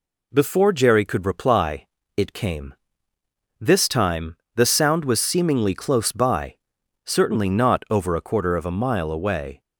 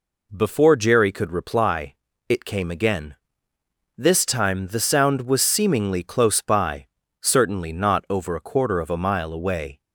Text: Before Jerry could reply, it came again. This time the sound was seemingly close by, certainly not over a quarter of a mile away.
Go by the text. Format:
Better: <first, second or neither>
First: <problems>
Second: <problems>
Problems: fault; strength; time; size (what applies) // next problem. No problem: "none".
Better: second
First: skips "again"; at 3.1 s // pauses between "time" and "the"; slight; at 4.3 s; 0.22 s long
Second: none